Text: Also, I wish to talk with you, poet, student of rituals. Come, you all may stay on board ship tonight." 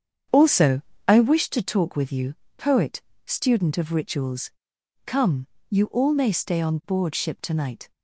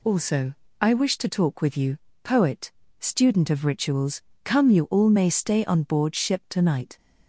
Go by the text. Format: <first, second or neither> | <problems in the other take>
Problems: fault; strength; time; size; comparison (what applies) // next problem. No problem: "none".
second | starts louder than the rest; strong; until 1.5 s; 8 dB